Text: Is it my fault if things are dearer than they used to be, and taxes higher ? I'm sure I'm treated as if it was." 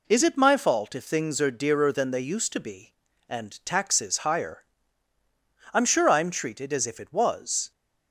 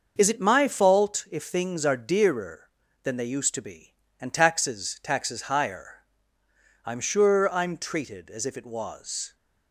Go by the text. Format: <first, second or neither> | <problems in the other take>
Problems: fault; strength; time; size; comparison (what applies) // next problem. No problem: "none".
first | starts louder than the rest; until 1.1 s; 6.5 dB // says "taxes" twice; at 5.0 s